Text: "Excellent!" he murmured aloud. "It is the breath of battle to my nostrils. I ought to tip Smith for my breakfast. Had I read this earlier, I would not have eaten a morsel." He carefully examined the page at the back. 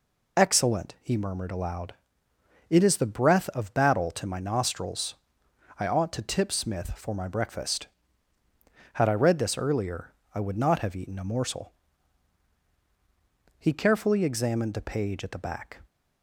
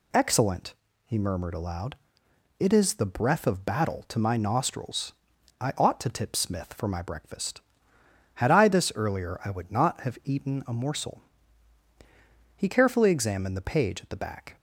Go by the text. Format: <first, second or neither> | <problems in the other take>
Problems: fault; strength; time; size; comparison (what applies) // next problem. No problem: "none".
first | skips "read"; at 8.6 s